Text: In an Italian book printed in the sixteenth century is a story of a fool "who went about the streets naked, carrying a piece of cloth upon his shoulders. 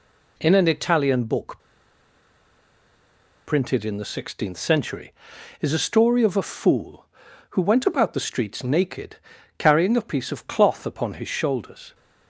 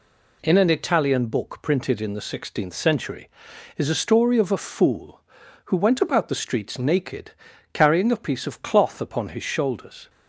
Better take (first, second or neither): second